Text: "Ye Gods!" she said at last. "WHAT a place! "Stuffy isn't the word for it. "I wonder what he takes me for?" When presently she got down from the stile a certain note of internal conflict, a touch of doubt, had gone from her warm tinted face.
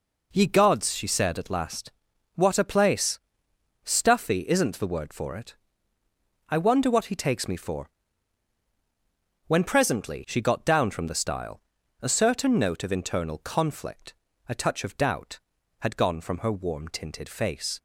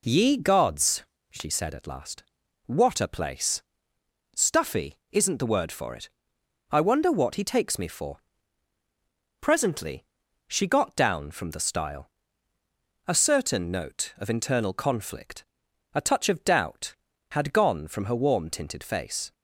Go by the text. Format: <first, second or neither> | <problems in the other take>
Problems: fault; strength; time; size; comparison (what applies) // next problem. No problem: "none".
first | skips "When"; at 8.8 s // pauses between "presently" and "she"; at 10.0 s; 0.42 s long // pauses between "stile" and "a"; noticeable; at 12.0 s; 0.98 s long; also in the first